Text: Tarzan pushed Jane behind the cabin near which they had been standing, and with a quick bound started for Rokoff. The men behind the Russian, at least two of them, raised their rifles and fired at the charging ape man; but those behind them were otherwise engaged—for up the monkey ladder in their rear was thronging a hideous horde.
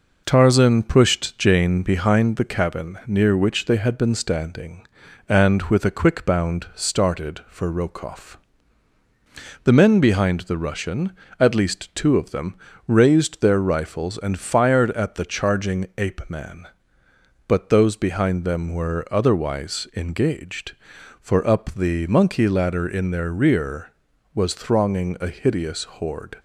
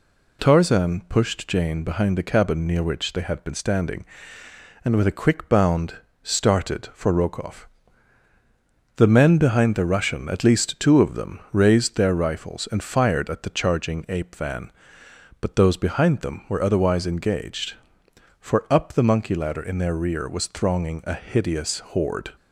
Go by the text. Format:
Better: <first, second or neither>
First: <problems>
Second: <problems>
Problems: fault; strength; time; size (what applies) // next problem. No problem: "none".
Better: first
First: none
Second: pauses between "bound" and "started"; slight; at 5.9 s; 0.26 s long // says "van" for "man"; at 14.3 s